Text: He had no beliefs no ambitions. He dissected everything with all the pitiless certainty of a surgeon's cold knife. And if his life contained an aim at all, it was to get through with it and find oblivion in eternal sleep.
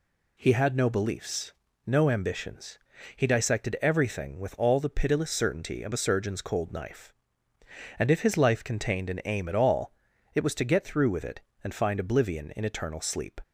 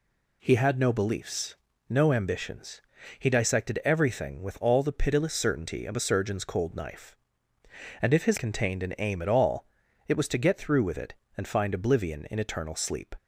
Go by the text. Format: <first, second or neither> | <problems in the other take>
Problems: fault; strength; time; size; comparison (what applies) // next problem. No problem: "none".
first | pauses between "beliefs" and "no"; at 1.5 s; 0.38 s long; also in the first // skips "life"; at 8.3 s